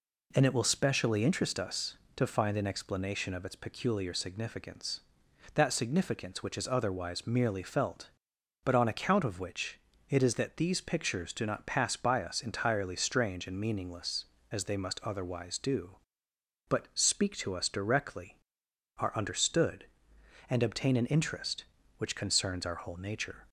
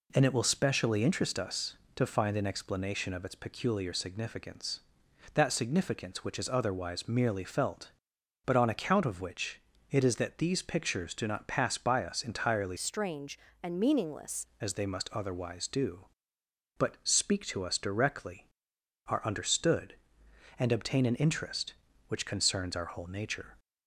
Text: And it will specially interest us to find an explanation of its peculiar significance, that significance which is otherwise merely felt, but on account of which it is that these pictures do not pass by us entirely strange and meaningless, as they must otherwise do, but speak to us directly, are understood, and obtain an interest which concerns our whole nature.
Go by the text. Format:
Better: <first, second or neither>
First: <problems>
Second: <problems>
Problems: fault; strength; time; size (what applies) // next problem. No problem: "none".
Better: first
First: pauses between "which" and "it"; slight; at 9.7 s; 0.28 s long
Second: pauses between "which" and "it"; slight; at 9.6 s; 0.28 s long // changes voice from "strange" to "meaningless"; from 12.7 to 14.4 s; 1.7 s long